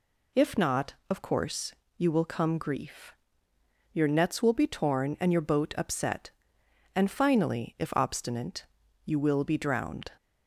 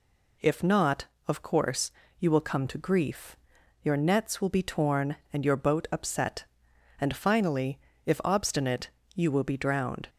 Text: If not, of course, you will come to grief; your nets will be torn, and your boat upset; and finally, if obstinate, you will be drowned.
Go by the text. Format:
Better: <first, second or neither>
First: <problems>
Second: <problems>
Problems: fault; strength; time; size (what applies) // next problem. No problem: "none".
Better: second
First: skips "to"; at 2.5 s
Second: none